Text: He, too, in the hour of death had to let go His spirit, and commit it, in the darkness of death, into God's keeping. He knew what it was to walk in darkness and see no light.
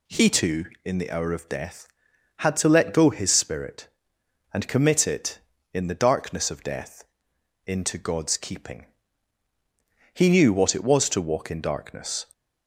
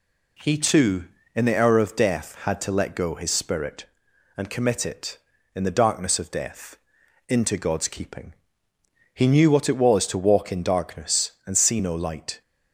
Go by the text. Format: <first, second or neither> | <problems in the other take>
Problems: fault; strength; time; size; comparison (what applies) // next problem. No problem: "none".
second | stops before "and see no light"; at 12.3 s